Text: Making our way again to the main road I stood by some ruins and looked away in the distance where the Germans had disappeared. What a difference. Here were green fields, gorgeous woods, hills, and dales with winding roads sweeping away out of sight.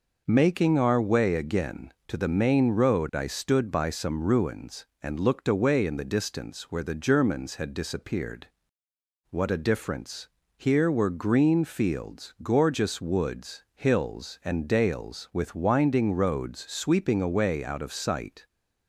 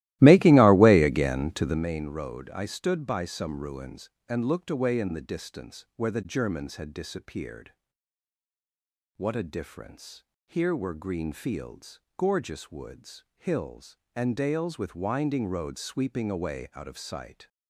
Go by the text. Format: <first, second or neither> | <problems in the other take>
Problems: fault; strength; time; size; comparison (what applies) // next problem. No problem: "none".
first | starts louder than the rest; strong; until 1.8 s; 16.5 dB